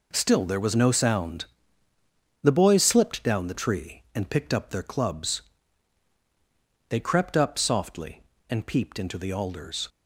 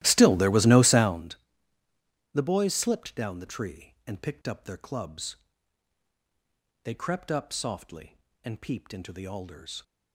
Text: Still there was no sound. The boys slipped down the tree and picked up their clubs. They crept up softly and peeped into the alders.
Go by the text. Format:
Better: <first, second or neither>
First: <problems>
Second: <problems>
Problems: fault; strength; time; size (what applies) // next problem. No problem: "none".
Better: first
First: none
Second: starts louder than the rest; strong; until 1.3 s; 15 dB